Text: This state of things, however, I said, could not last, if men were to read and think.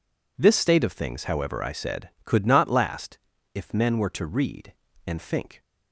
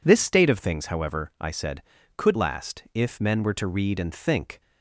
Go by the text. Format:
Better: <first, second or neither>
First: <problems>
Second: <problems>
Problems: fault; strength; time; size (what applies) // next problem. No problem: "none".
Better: first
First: none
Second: skips "not"; at 2.3 s